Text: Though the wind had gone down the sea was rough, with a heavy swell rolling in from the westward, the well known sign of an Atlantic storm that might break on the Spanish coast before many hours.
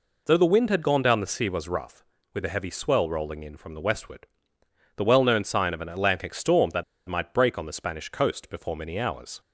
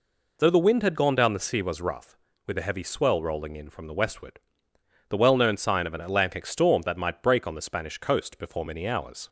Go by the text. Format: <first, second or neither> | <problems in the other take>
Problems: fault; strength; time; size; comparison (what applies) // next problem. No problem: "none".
second | pauses between "that" and "might"; slight; at 6.8 s; 0.24 s long